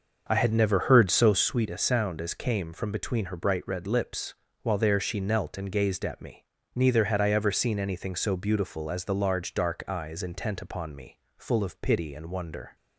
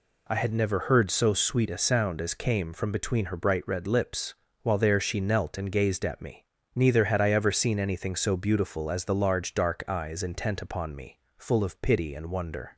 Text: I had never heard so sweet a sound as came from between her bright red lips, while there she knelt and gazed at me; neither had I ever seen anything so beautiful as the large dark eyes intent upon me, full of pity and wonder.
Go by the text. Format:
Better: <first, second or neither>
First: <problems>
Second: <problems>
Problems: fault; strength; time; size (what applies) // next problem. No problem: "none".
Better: second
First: starts louder than the rest; until 1.5 s; 6.5 dB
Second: none